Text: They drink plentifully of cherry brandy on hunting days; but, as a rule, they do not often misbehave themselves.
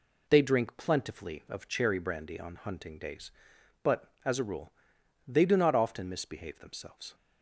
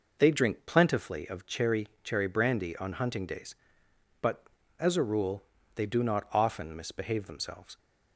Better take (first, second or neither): first